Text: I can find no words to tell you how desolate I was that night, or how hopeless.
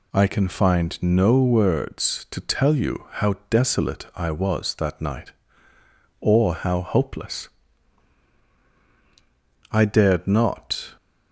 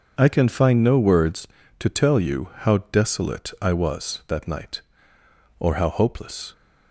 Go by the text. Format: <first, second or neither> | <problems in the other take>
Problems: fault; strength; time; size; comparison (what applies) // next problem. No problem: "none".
second | goes on to say "I dared not"; noticeable; from 9.7 s on; 1.2 s long